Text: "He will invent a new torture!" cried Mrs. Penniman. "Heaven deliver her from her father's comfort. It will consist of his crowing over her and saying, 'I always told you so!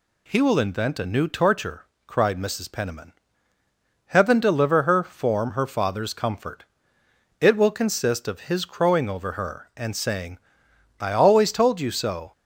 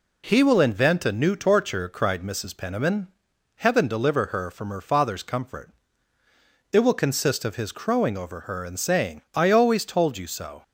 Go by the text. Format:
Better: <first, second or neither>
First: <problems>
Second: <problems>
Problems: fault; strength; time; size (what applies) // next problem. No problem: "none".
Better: second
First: says "form" for "from"; at 5.0 s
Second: none